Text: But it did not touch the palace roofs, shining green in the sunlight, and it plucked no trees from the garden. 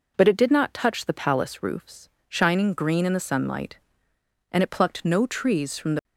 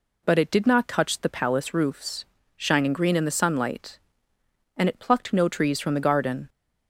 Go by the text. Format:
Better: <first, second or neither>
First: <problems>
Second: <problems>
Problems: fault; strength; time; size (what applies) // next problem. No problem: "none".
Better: second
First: stops before "garden"; at 6.0 s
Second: none